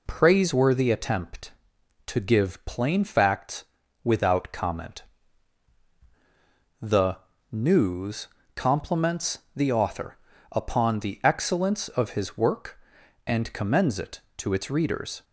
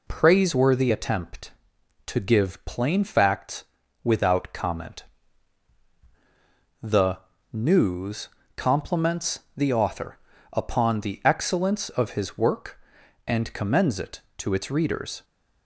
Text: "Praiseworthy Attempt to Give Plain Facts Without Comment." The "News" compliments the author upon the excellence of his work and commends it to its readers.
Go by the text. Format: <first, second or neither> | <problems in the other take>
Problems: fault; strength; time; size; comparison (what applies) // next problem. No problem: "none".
neither | pauses between "Facts" and "Without"; the same in both // pauses between "The" and "News"; slight; the same in both // pauses between "News" and "compliments"; slight; the same in both // pauses between "compliments" and "the"; slight; the same in both // pauses between "author" and "upon"; slight; the same in both